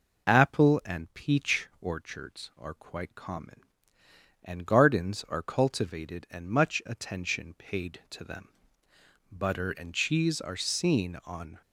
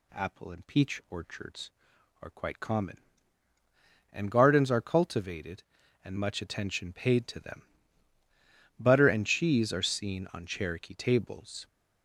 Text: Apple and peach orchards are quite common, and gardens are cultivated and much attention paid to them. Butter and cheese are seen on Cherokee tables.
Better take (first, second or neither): second